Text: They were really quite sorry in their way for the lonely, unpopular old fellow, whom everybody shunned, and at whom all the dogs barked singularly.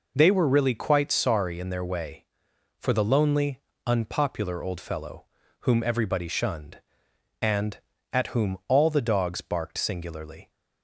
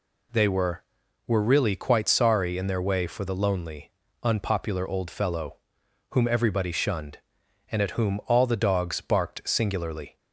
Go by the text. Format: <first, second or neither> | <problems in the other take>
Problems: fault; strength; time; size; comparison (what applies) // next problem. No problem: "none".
first | says "were" twice; at 1.2 s